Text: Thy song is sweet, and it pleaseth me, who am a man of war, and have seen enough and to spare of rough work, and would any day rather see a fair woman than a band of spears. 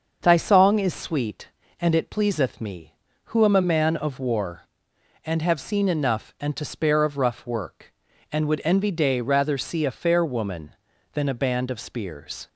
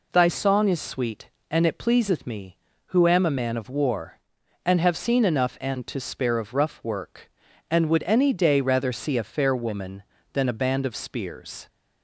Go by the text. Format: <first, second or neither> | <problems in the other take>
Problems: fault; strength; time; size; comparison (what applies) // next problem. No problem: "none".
second | starts louder than the rest; until 1.2 s; 6.5 dB // says "envy" for "any"; at 8.6 s